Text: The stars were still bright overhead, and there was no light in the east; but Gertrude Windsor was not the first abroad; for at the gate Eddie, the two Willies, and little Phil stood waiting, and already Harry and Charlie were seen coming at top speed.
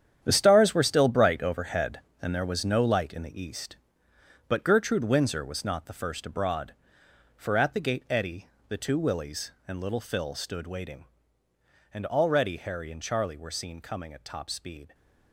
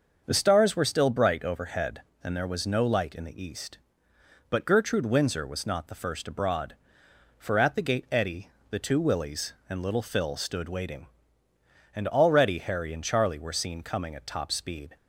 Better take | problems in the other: second | gets quieter; strong; throughout; 11.5 dB // starts louder than the rest; strong; until 1.2 s; 9 dB; also in the second

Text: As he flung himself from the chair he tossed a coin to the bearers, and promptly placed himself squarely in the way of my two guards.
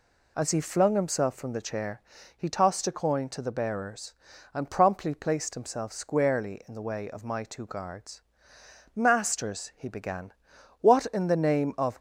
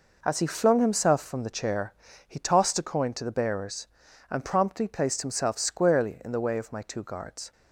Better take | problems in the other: second | pauses between "chair" and "he"; slight; at 2.0 s; 0.34 s long; slight in the second // goes on to say "Masters he began what in the name of"; strong; from 8.9 s on; 3.0 s long

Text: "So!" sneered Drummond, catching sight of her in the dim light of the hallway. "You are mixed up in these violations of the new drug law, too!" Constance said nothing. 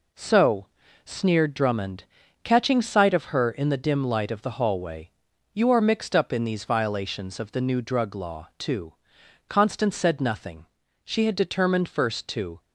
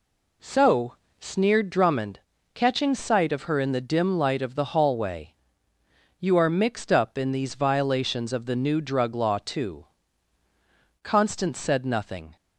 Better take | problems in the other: second | goes on to say "She had determined first to"; from 11.0 s on; 1.5 s long

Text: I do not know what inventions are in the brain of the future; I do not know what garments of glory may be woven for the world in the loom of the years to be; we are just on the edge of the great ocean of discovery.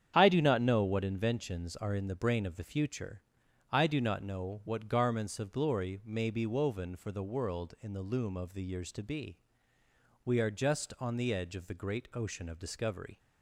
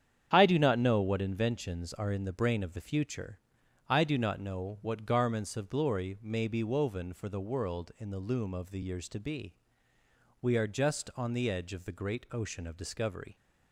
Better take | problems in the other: neither | starts louder than the rest; strong; the same in both

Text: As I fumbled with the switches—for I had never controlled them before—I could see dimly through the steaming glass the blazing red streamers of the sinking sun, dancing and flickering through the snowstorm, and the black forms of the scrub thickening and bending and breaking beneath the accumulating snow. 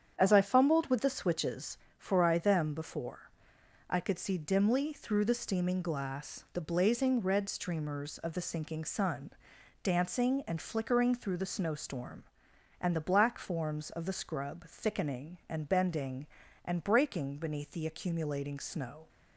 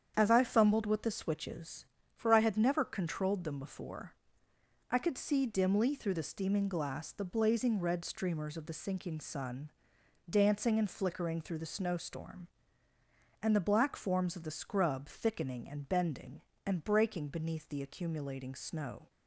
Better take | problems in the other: second | starts louder than the rest; strong; until 1.1 s; 8.5 dB; strong in the second // skips "had never controlled"; at 2.3 s

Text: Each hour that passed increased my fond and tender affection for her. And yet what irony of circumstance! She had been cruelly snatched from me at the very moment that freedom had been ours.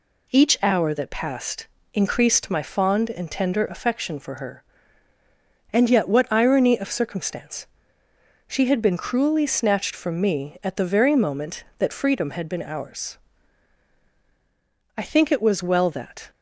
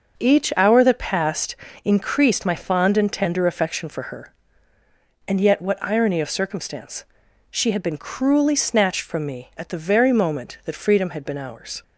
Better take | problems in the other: second | pauses between "passed" and "increased"; slight; at 1.6 s; 0.26 s long; slight in the second // goes on to say "I think it was well that"; from 14.9 s on; 1.3 s long

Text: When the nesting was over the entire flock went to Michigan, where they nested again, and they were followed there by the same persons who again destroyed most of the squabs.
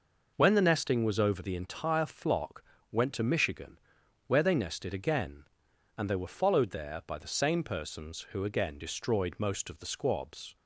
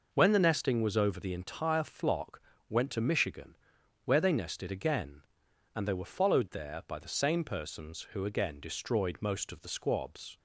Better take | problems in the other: neither | pauses between "flock" and "went"; slight; the same in both

